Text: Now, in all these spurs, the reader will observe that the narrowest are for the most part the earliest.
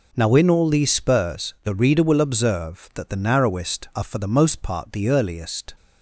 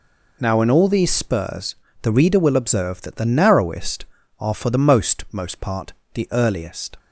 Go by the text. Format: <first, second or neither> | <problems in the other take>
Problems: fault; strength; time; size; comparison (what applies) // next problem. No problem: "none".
first | says "most" twice; at 5.3 s // pauses between "part" and "the"; slight; at 5.9 s; 0.20 s long